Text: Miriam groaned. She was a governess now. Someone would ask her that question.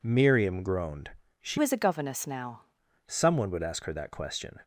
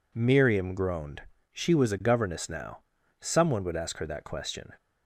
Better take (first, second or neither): second